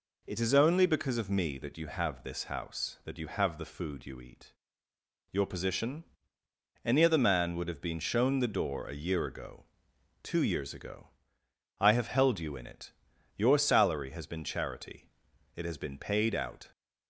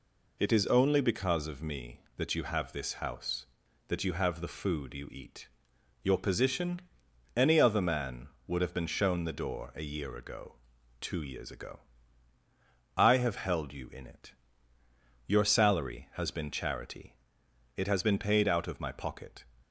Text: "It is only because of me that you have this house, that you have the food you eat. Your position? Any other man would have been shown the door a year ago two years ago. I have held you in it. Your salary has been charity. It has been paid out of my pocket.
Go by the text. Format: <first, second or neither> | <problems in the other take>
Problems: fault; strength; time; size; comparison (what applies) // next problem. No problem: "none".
second | pauses between "ago" and "two"; noticeable; at 9.6 s; 0.56 s long; also in the second // stops before "of my pocket"; at 16.7 s